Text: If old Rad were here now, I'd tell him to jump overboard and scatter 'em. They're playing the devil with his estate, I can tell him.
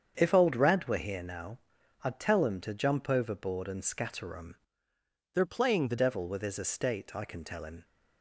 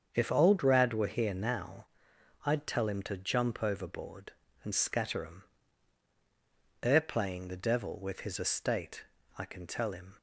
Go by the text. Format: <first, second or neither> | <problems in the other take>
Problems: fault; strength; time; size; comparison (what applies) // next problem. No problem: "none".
second | starts louder than the rest; strong; until 1.1 s; 7.5 dB; also in the second // changes voice from "They're" to "the"; from 5.3 to 5.9 s; 0.6 s long